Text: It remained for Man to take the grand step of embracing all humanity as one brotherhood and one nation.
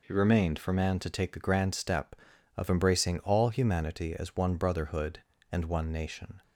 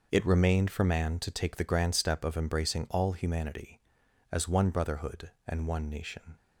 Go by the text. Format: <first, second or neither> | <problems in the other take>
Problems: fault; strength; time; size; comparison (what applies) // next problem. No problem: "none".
neither | none